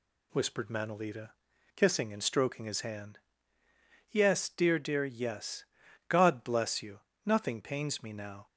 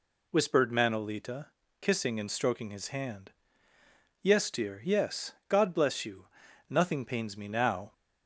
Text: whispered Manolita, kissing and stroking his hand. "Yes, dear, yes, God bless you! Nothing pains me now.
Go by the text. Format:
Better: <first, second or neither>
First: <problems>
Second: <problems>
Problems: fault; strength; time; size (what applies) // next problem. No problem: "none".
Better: second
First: says "dear" twice; at 4.7 s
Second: none